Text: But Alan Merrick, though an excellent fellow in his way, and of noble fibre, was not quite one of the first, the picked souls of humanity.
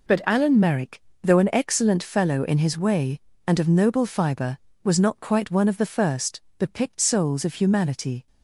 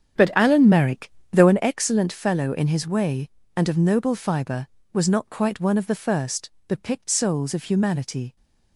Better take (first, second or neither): first